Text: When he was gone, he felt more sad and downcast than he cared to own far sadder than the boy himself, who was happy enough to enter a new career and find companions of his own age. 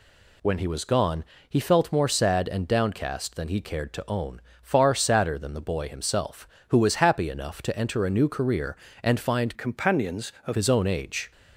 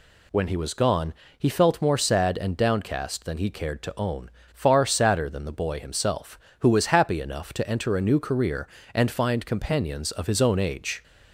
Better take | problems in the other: second | pauses between "own" and "far"; slight; at 4.3 s; 0.22 s long; slight in the second // changes voice from "companions" to "of"; from 9.5 to 10.5 s; 1.0 s long

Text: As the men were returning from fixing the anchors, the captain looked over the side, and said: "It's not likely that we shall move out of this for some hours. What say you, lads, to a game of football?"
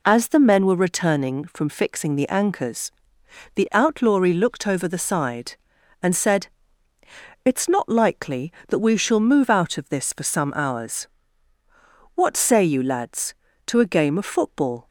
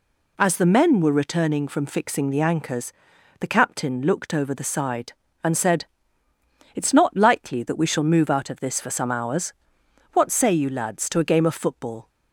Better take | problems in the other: second | says "outlawry" for "captain"; at 3.7 s

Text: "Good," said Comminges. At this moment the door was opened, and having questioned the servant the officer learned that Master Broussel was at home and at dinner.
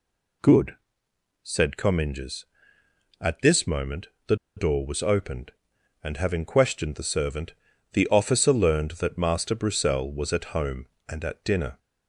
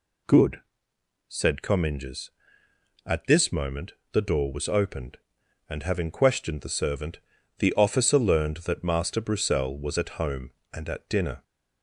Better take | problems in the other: second | pauses between "moment" and "the"; slight; at 4.0 s; 0.20 s long; slight in the second // pauses between "the" and "door"; slight; at 4.3 s; 0.21 s long // pauses between "servant" and "the"; at 7.5 s; 0.40 s long; also in the second

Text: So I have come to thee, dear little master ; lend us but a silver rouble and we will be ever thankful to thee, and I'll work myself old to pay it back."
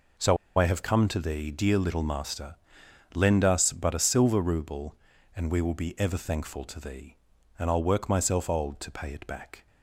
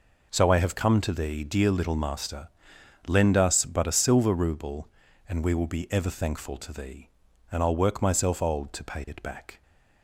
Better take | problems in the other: second | pauses between "So" and "I"; slight; at 0.3 s; 0.21 s long

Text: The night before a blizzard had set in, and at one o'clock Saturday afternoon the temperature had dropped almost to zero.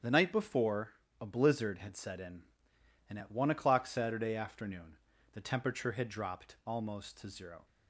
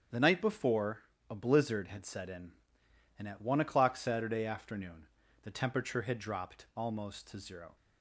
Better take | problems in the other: neither | starts louder than the rest; strong; the same in both // pauses between "before" and "a"; slight; the same in both // pauses between "afternoon" and "the"; slight; the same in both

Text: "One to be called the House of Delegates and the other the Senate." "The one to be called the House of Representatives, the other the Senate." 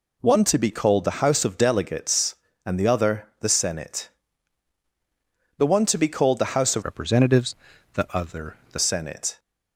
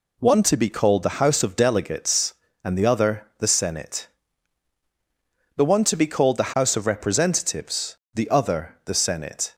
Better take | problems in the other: second | changes voice from "Representatives" to "the"; from 6.8 to 8.7 s; 1.9 s long // pauses between "other" and "the"; slight; at 8.5 s; 0.16 s long

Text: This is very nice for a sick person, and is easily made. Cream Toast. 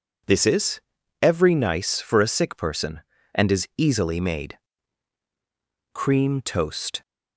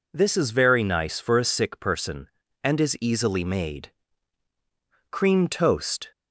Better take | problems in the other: second | says "every" for "very"; at 1.2 s

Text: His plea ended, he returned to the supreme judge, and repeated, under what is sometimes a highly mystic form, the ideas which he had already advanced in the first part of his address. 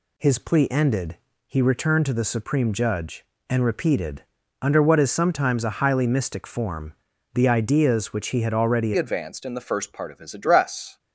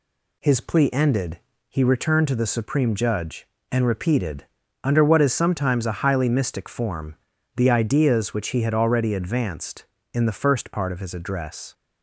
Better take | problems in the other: second | changes voice at "advanced"; from 8.9 s on; 2.0 s long

